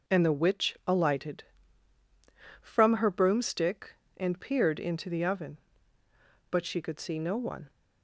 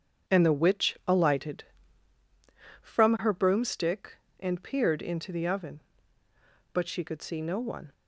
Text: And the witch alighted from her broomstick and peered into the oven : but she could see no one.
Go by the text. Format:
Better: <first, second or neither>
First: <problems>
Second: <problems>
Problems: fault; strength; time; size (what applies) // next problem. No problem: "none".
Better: first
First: none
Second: starts louder than the rest; strong; until 2.2 s; 7.5 dB